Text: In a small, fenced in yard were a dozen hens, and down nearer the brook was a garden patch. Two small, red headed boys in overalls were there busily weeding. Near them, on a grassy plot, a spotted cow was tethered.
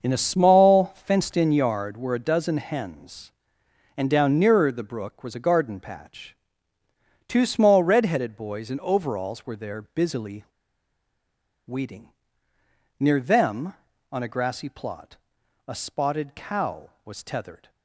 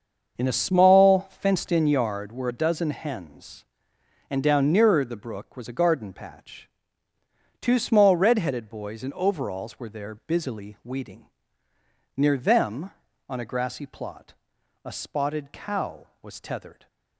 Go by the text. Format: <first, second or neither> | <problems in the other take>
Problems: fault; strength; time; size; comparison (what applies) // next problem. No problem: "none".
second | starts louder than the rest; until 1.0 s; 6.5 dB; also in the second // pauses between "busily" and "weeding"; at 10.4 s; 1.2 s long